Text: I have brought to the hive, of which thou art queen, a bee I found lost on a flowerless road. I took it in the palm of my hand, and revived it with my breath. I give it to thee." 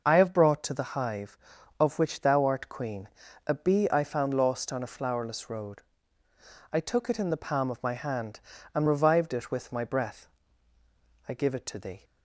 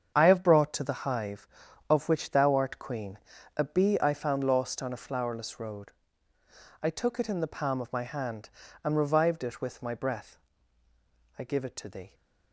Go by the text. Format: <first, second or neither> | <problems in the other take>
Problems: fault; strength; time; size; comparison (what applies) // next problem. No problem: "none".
first | gets quieter; strong; throughout; 10 dB